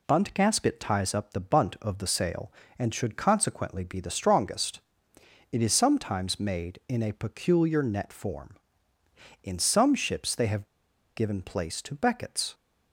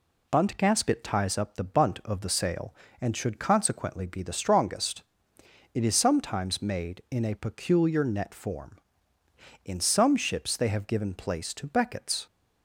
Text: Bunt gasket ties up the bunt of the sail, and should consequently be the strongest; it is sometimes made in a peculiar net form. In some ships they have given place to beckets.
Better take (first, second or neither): second